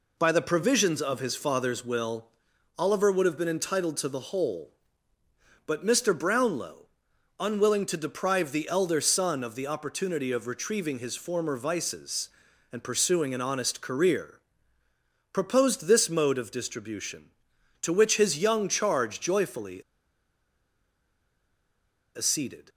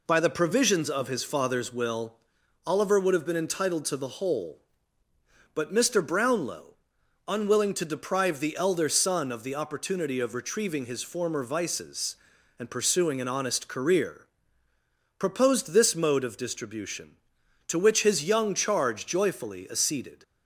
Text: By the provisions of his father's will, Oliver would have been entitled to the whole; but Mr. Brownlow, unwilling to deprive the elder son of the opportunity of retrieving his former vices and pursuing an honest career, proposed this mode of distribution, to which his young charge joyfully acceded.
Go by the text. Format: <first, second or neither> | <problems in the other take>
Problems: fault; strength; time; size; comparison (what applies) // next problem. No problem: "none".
second | pauses between "joyfully" and "acceded"; strong; at 19.8 s; 2.3 s long